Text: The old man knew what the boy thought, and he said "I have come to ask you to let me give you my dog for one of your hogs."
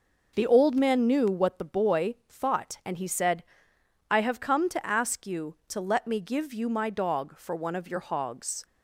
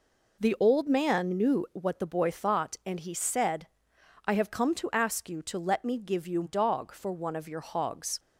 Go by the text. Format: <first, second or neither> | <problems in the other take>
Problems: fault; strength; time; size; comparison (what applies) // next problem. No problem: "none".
first | pauses between "said" and "I"; noticeable; at 3.6 s; 0.58 s long; noticeable in the first // skips "my"; at 6.4 s